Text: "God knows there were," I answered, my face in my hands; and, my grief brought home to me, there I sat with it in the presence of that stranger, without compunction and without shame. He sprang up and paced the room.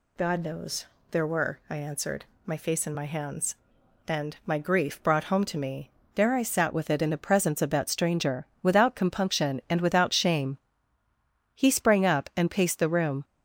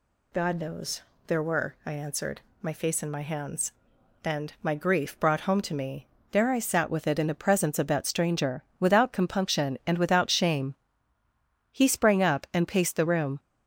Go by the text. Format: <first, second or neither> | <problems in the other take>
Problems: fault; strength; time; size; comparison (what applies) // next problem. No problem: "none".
neither | pauses between "knows" and "there"; slight; the same in both